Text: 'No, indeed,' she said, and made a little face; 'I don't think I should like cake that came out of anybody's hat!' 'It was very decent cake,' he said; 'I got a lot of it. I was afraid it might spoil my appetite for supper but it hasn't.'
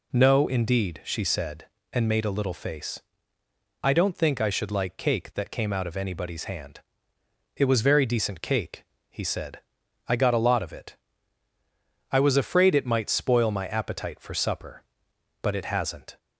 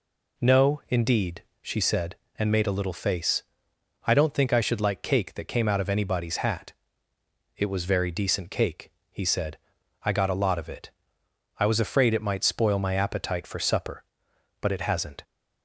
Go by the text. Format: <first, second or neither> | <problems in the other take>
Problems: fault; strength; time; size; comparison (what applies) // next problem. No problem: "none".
second | says "hand" for "hat"; at 6.4 s